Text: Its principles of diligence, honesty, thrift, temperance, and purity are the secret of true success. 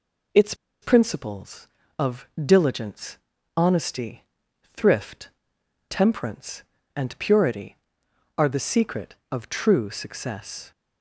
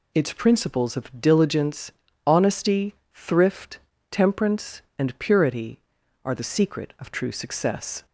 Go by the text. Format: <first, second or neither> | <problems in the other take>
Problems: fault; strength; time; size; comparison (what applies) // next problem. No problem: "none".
second | pauses between "Its" and "principles"; slight; at 0.5 s; 0.28 s long // pauses between "of" and "diligence"; slight; at 2.2 s; 0.16 s long